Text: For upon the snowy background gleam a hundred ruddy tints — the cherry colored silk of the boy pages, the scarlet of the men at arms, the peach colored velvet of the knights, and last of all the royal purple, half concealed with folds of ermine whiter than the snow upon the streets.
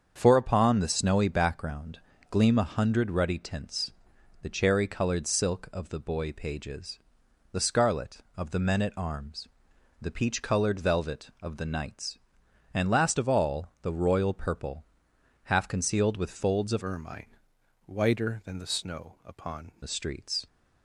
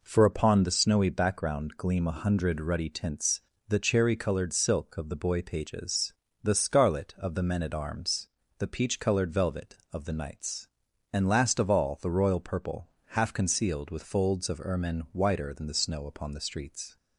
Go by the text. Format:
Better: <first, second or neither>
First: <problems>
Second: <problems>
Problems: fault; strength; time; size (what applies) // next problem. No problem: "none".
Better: second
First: starts louder than the rest; strong; until 1.2 s; 7 dB // pauses between "background" and "gleam"; slight; at 1.9 s; 0.32 s long // changes voice from "ermine" to "upon"; from 16.8 to 19.7 s; 2.9 s long // pauses between "ermine" and "whiter"; noticeable; at 17.3 s; 0.52 s long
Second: none